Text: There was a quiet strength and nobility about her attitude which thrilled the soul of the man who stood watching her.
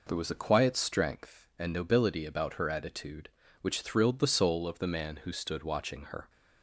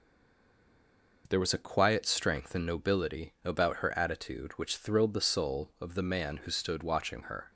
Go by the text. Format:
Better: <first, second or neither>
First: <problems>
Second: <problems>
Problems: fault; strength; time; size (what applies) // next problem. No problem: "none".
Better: first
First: none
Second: stays silent before the first word; noticeable; until 1.2 s; 1.2 s long